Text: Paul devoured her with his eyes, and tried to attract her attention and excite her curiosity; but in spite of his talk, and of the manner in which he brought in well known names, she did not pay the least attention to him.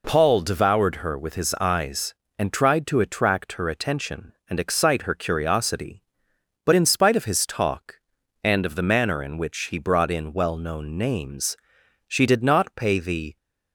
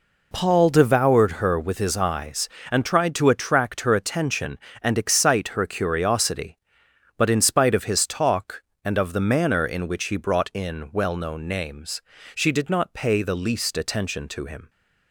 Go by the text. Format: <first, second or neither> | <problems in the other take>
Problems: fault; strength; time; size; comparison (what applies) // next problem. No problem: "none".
second | stops before "least attention to him"; at 13.3 s